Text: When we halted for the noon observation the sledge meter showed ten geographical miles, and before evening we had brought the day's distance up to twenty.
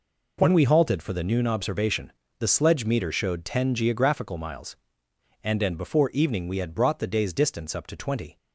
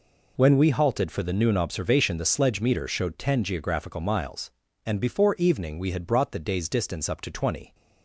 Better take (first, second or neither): second